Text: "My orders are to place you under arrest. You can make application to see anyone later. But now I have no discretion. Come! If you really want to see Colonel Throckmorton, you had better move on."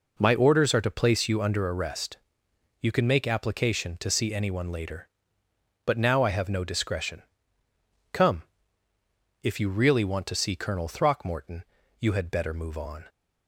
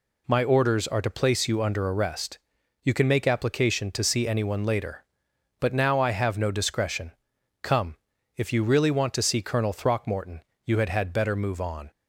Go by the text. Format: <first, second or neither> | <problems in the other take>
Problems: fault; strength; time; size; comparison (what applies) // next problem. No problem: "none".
first | says "had" twice; at 10.8 s